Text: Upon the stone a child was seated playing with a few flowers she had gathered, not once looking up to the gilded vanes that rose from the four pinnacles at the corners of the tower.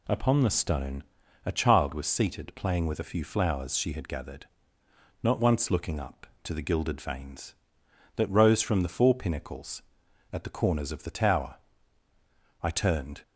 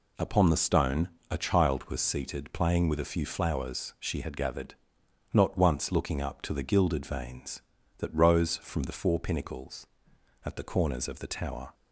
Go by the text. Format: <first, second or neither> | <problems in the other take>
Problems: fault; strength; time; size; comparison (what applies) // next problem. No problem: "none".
second | pauses between "stone" and "a"; at 1.0 s; 0.44 s long; slight in the second // goes on to say "I turned"; from 12.6 s on; 0.60 s long